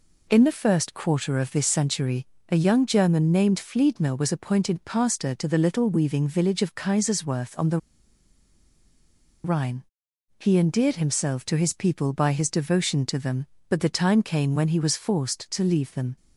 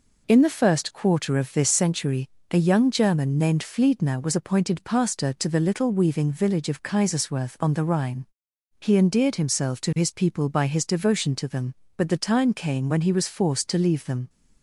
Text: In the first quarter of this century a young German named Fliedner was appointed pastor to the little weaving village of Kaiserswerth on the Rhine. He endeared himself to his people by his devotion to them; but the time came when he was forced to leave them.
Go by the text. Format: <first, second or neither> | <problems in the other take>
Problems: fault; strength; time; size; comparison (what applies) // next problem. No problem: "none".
second | pauses between "century" and "a"; slight; at 2.2 s; 0.24 s long; slight in the second // pauses between "the" and "Rhine"; strong; at 7.7 s; 1.6 s long